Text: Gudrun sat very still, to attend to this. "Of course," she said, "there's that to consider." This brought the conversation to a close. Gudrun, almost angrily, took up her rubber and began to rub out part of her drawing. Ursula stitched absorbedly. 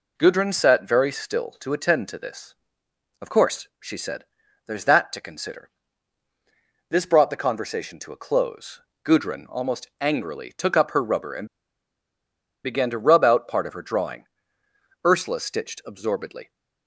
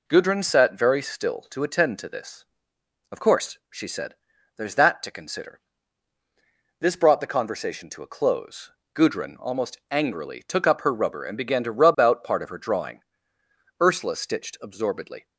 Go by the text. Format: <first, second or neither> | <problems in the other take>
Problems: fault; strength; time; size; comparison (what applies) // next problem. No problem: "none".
second | pauses between "and" and "began"; at 11.4 s; 1.1 s long